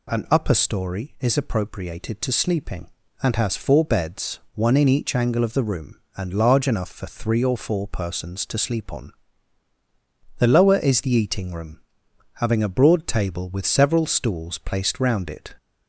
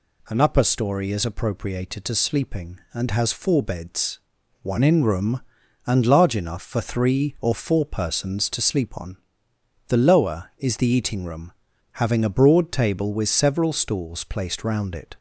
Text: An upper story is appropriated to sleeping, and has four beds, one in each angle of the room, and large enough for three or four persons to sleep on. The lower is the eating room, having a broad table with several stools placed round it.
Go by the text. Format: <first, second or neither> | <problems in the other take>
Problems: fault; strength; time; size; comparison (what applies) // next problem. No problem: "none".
first | skips "each angle of the"; at 5.0 s